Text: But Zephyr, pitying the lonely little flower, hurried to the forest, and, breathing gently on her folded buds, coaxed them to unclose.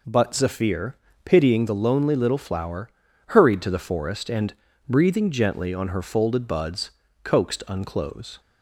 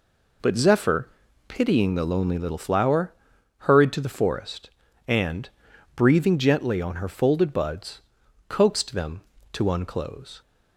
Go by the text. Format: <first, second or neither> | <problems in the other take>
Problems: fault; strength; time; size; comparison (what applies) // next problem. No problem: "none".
second | skips "them to"; at 7.6 s